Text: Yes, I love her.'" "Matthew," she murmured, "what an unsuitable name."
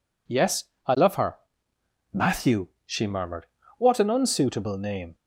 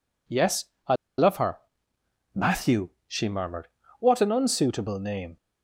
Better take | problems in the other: first | pauses between "I" and "love"; slight; at 0.9 s; 0.22 s long

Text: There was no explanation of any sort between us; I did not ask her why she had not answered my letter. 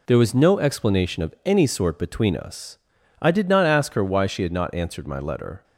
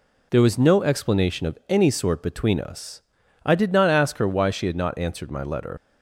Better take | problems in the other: first | leaves "letter" unfinished; at 5.7 s; 100 ms

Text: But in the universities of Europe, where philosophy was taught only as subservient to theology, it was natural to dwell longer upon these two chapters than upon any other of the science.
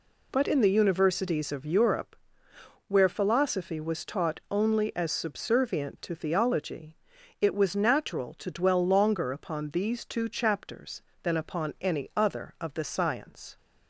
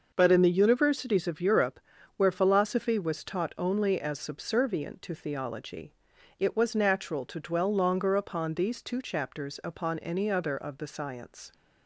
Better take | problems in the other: first | skips "than"; at 9.6 s

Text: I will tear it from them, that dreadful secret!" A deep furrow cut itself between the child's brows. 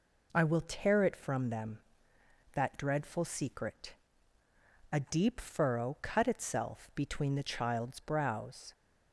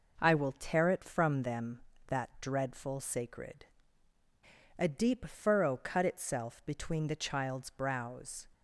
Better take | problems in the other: first | says "sacred" for "secret"; at 3.0 s

